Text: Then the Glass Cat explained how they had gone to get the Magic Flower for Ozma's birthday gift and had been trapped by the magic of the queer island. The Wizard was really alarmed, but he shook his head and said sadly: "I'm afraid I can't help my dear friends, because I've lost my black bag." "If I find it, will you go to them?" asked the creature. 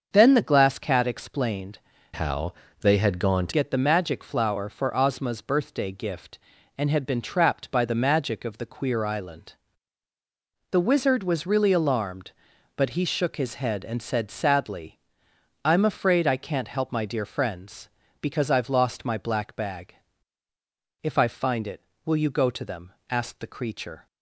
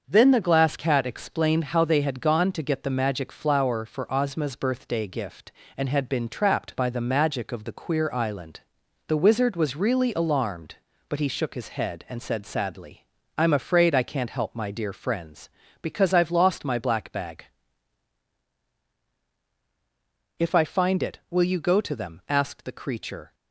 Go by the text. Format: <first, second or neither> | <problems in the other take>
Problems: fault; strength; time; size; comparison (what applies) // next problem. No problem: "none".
second | starts louder than the rest; until 1.1 s; 6.5 dB; also in the second // changes voice from "how" to "to"; from 2.1 to 3.5 s; 1.4 s long // pauses between "how" and "they"; slight; at 2.5 s; 0.28 s long